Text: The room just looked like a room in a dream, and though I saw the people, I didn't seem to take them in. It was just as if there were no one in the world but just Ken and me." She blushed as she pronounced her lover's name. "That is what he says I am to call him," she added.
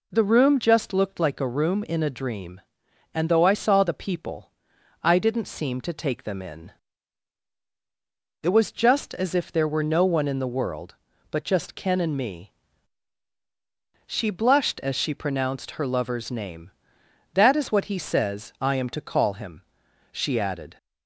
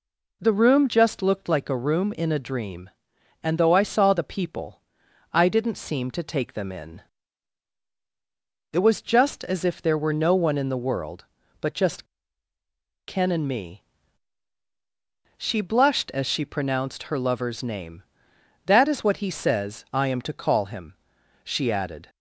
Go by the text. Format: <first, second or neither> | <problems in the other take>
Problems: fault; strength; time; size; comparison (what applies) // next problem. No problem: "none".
first | pauses between "just" and "Ken"; at 12.0 s; 1.0 s long